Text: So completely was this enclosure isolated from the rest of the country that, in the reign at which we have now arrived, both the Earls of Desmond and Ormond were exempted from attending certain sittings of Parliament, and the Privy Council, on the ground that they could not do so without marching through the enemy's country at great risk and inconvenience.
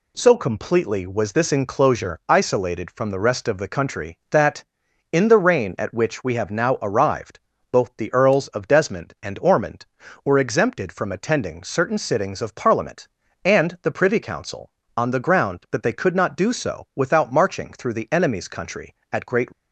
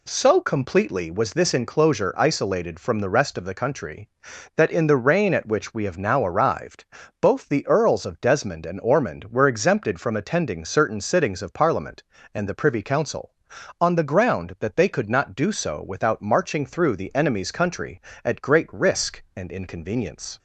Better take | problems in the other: second | stops before "risk and inconvenience"; at 19.5 s

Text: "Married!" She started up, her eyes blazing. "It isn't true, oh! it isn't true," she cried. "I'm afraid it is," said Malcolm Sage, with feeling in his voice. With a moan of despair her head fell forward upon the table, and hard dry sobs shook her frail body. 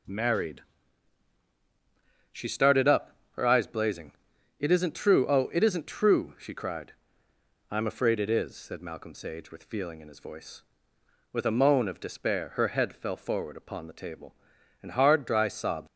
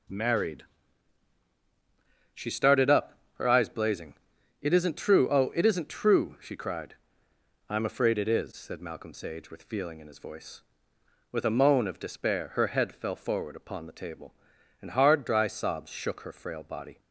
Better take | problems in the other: second | stops before "shook her frail body"; at 15.8 s

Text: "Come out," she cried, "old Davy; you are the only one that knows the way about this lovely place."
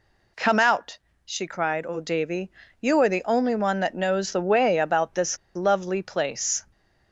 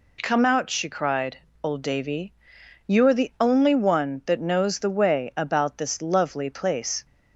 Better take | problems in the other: second | pauses between "this" and "lovely"; slight; at 5.3 s; 0.18 s long

